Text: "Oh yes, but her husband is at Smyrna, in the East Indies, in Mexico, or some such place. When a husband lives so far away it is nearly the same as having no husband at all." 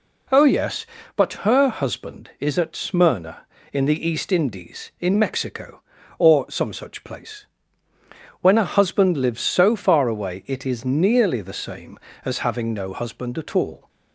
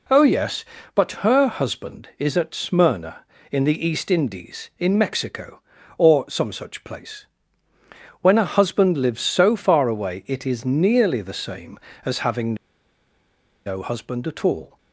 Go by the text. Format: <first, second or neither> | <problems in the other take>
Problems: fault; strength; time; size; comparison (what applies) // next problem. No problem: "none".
first | pauses between "having" and "no"; at 12.5 s; 1.1 s long